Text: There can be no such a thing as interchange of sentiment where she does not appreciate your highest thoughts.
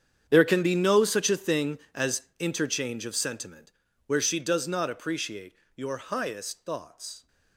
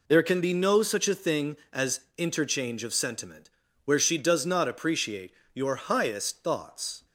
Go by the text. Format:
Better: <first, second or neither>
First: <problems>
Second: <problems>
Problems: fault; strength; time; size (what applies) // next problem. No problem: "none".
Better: second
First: gets quieter; strong; throughout; 17 dB // pauses between "as" and "interchange"; slight; at 2.2 s; 0.16 s long // pauses between "sentiment" and "where"; slight; at 3.7 s; 0.36 s long // pauses between "appreciate" and "your"; slight; at 5.5 s; 0.20 s long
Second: pauses between "as" and "interchange"; slight; at 2.0 s; 0.16 s long // pauses between "sentiment" and "where"; slight; at 3.4 s; 0.36 s long // pauses between "appreciate" and "your"; slight; at 5.3 s; 0.20 s long